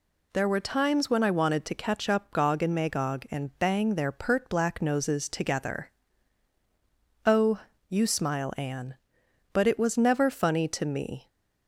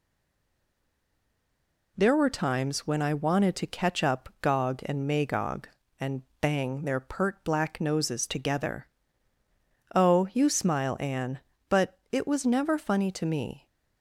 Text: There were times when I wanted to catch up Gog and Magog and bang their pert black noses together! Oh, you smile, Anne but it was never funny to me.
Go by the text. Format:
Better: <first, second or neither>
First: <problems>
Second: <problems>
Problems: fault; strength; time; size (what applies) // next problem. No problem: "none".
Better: first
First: none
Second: stays silent before the first word; noticeable; until 1.9 s; 1.9 s long // pauses between "and" and "bang"; slight; at 6.2 s; 0.18 s long